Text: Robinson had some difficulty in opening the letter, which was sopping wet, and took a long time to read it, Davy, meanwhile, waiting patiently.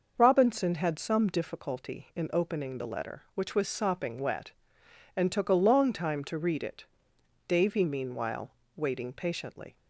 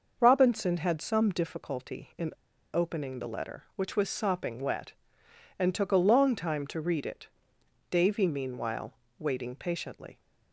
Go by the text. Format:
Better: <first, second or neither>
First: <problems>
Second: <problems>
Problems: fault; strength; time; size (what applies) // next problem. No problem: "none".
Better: first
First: starts louder than the rest; noticeable; until 1.1 s; 6 dB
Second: starts louder than the rest; noticeable; until 1.2 s; 6 dB // pauses between "in" and "opening"; at 2.3 s; 0.42 s long